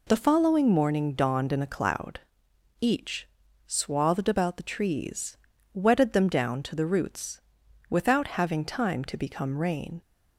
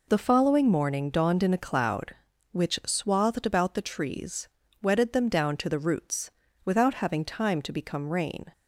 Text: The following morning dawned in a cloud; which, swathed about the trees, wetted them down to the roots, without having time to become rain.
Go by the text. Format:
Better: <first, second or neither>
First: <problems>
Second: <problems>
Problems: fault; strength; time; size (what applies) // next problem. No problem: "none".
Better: second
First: says "each" for "which"; at 2.7 s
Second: none